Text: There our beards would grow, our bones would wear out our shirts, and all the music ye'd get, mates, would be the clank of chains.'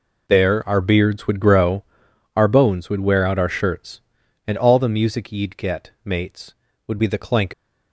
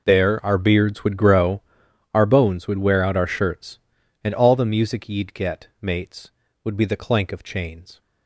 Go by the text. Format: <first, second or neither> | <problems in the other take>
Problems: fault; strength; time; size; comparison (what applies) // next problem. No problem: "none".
second | stops before "of chains"; at 7.5 s